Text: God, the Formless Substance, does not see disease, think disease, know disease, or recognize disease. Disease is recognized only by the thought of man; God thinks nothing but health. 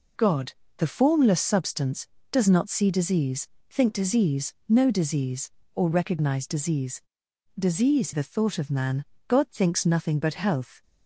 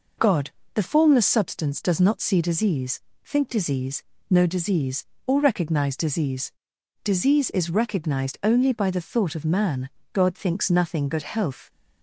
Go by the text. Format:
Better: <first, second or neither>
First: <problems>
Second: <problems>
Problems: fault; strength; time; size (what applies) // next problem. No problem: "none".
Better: second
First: skips "is recognized only by"; at 8.1 s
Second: none